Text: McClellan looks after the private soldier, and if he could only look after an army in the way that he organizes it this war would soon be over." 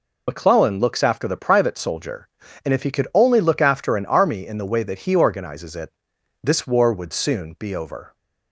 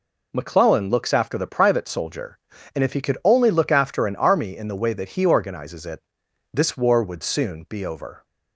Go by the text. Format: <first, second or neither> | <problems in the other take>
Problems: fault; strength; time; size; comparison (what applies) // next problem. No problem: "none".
second | loses the start of "McClellan"; at 0.2 s; 50 ms // pauses between "it" and "this"; noticeable; at 5.9 s; 0.52 s long; noticeable in the second